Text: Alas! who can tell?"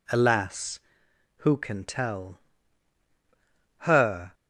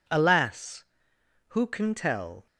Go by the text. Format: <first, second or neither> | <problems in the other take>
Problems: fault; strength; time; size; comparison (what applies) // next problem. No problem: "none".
second | goes on to say "Her"; from 3.7 s on; 0.56 s long